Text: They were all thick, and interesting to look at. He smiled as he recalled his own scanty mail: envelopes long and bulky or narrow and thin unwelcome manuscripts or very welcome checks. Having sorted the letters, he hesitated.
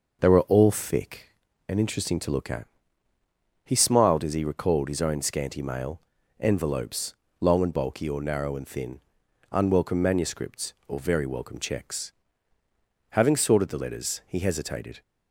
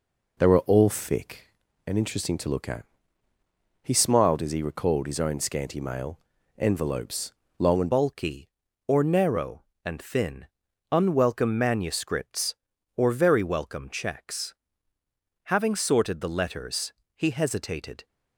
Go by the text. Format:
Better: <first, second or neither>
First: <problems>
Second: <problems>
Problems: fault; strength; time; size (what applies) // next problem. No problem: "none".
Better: first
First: pauses between "envelopes" and "long"; slight; at 7.1 s; 0.24 s long // pauses between "thin" and "unwelcome"; noticeable; at 8.9 s; 0.54 s long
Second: pauses between "envelopes" and "long"; slight; at 7.3 s; 0.24 s long // changes voice at "bulky"; from 7.9 s on; 10.1 s long // pauses between "thin" and "unwelcome"; at 10.4 s; 0.44 s long